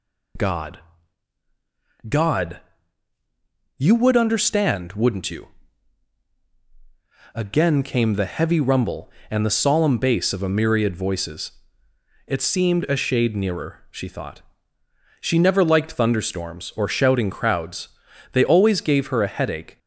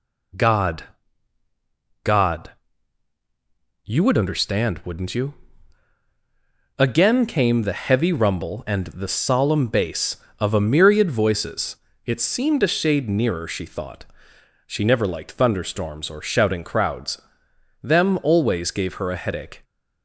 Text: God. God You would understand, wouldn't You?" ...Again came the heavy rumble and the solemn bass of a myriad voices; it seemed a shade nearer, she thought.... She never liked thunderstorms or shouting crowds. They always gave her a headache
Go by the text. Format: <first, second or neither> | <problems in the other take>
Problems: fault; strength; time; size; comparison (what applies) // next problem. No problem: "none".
first | pauses between "God" and "You"; strong; at 2.5 s; 1.3 s long; also in the first // says "Them" for "They"; at 17.8 s